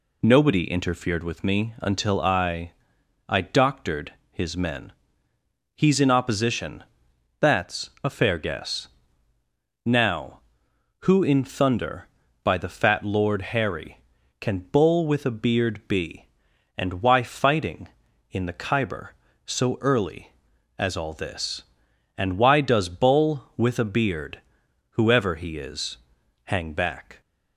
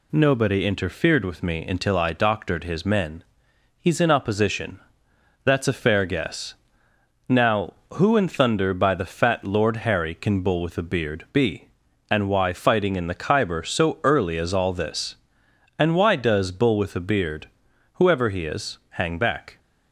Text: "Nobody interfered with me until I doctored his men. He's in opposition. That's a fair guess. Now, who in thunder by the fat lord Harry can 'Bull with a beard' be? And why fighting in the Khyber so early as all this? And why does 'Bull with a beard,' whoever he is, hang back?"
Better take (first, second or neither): second